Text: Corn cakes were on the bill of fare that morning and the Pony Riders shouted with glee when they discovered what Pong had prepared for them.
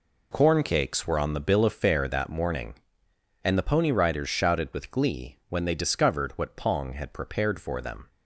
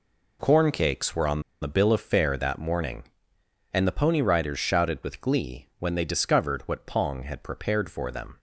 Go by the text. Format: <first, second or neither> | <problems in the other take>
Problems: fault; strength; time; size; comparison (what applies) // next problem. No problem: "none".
first | pauses between "on" and "the"; slight; at 1.4 s; 0.19 s long